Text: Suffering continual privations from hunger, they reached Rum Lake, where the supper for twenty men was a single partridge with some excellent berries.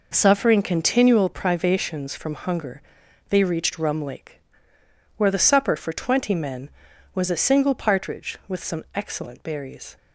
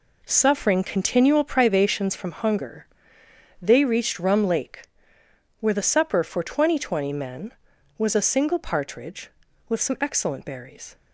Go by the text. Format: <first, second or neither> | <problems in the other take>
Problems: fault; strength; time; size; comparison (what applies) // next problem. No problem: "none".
first | says "twenty" twice; at 6.7 s